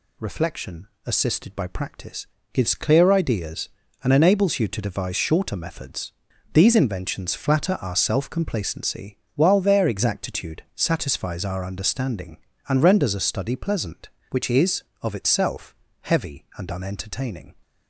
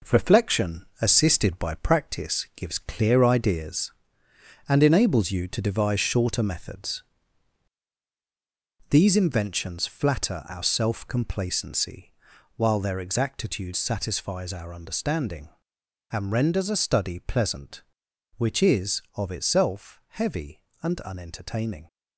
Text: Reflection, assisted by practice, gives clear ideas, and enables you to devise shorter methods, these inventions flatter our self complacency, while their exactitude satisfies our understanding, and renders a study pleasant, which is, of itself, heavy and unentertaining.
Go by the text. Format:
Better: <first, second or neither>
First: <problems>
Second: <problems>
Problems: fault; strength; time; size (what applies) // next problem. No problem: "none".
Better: first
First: none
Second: gets quieter; strong; throughout; 7 dB